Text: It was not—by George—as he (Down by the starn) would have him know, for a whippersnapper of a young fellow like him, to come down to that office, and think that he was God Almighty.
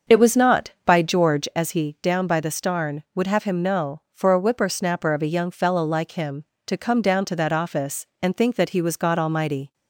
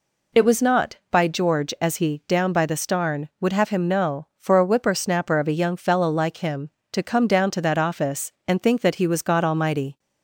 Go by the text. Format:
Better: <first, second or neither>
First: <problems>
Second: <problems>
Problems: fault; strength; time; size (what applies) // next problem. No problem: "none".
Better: second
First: starts louder than the rest; until 1.5 s; 7 dB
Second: none